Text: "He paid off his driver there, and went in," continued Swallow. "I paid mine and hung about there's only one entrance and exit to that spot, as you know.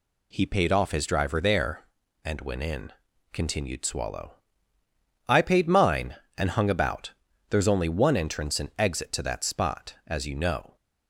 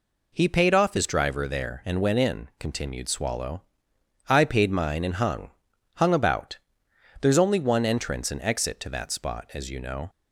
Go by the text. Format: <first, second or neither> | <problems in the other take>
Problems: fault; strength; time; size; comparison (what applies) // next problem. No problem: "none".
first | says "hung" twice; at 5.9 s // pauses between "about" and "there's"; noticeable; at 6.5 s; 0.64 s long; also in the first